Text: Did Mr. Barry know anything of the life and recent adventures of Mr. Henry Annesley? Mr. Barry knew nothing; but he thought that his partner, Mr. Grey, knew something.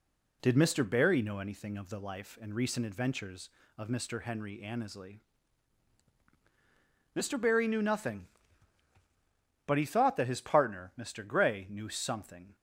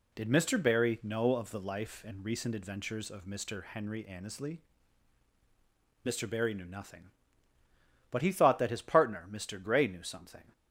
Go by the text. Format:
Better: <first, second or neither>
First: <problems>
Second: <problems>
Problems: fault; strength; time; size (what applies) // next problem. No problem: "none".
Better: first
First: none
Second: skips "anything"; at 1.3 s